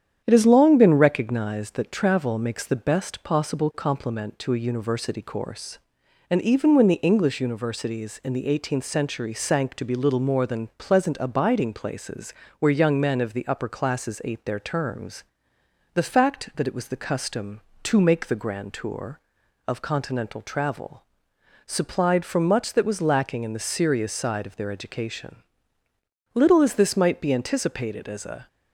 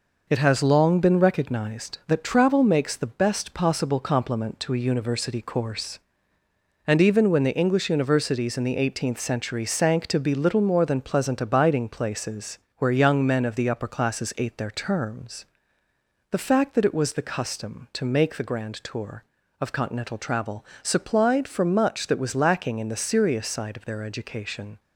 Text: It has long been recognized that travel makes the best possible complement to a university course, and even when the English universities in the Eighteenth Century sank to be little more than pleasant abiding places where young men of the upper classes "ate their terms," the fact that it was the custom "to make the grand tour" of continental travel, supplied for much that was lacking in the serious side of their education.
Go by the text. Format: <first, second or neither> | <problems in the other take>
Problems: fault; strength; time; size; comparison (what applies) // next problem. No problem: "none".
second | starts louder than the rest; strong; until 1.2 s; 9 dB // pauses between "places" and "where"; slight; at 12.3 s; 0.24 s long; slight in the second // goes on to say "Little as this might be anticipated as a"; strong; from 26.3 s on; 2.1 s long